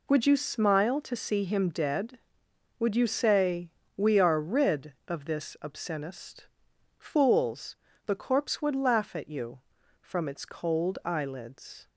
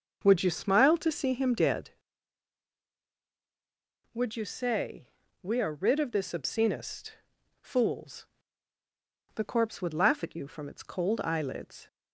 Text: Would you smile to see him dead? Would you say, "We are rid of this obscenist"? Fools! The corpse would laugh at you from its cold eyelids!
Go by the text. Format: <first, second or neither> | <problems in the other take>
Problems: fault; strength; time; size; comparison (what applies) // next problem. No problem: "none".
first | starts louder than the rest; noticeable; until 1.9 s; 6 dB